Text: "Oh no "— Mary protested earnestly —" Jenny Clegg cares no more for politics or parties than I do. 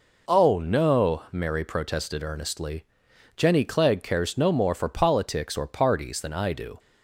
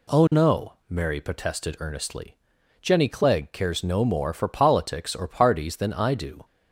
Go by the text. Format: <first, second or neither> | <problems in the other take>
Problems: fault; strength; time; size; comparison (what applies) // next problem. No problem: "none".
neither | none